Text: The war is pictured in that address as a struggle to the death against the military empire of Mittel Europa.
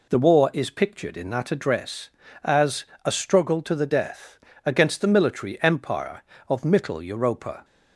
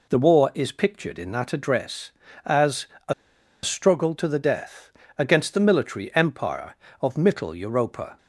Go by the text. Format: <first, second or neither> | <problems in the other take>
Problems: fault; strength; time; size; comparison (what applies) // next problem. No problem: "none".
first | pauses between "as" and "a"; slight; at 2.8 s; 0.22 s long; slight in the first // pauses between "a" and "struggle"; noticeable; at 3.1 s; 0.51 s long // pauses between "death" and "against"; slight; at 4.8 s; 0.28 s long; slight in the first